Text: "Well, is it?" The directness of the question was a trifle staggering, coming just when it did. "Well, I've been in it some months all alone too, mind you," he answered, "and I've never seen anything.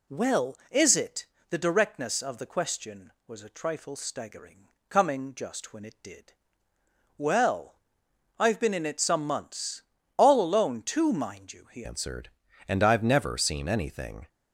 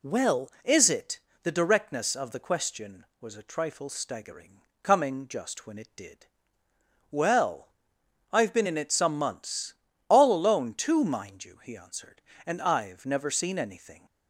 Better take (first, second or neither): second